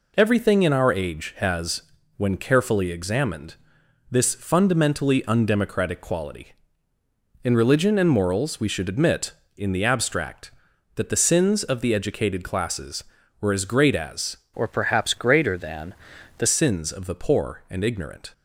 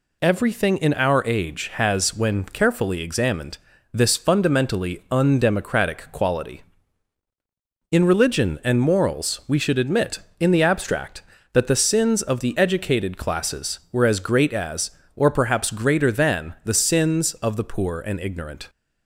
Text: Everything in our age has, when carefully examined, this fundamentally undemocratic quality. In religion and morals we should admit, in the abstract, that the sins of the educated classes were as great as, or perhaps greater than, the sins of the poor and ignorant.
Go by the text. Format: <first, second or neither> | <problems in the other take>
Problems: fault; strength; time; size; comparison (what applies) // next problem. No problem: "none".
second | changes voice from "or" to "the"; from 14.5 to 16.4 s; 1.9 s long